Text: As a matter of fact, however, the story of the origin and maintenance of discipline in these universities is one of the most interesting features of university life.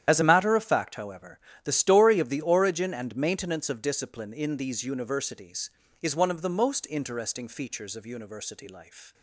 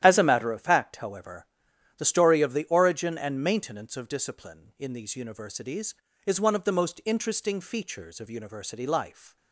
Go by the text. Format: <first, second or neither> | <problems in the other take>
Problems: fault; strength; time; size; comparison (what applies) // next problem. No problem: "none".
second | loses the start of "As"; at 0.0 s; 30 ms // starts louder than the rest; strong; until 1.0 s; 10.5 dB; strong in the second